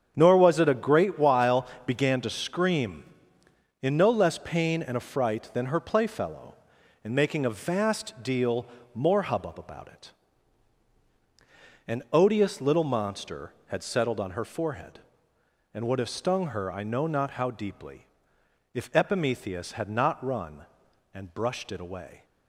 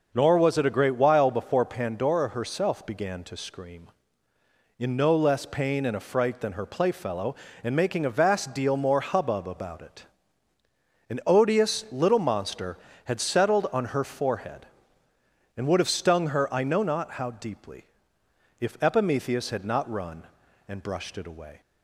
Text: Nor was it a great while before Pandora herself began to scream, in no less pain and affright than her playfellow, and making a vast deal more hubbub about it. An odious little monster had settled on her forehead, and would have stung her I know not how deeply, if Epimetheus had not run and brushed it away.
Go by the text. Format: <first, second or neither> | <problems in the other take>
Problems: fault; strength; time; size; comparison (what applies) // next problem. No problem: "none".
second | starts louder than the rest; strong; until 1.1 s; 8 dB // skips "before Pandora herself"; at 1.7 s // pauses between "deal" and "more"; slight; at 8.6 s; 0.28 s long